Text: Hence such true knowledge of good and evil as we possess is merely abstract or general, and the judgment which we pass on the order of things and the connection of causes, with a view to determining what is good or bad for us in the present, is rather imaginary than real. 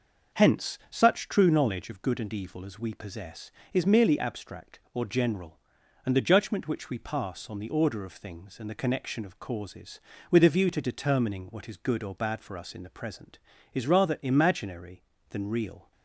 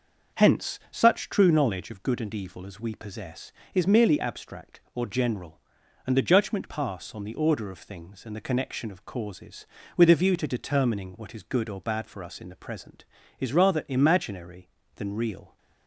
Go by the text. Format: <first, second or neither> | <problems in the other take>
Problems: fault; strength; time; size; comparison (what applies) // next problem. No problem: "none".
first | starts louder than the rest; until 1.4 s; 6 dB; noticeable in the first // skips "which we"; at 6.6 s